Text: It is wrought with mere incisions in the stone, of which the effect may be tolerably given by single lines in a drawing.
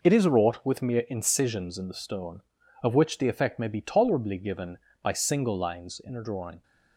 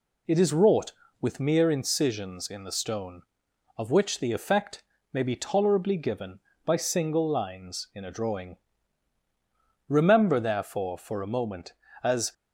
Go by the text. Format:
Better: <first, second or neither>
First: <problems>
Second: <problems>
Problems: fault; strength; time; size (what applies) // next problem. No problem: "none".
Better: first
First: none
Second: pauses between "effect" and "may"; slight; at 4.8 s; 0.28 s long // goes on to say "Remember therefore for a moment as"; strong; from 9.8 s on; 2.4 s long